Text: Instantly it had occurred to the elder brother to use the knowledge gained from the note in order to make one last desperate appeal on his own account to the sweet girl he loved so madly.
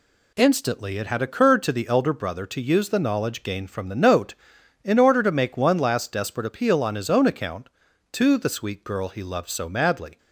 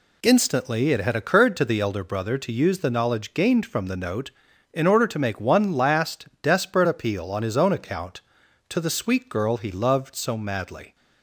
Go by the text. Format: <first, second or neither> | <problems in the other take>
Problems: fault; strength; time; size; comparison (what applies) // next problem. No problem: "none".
neither | none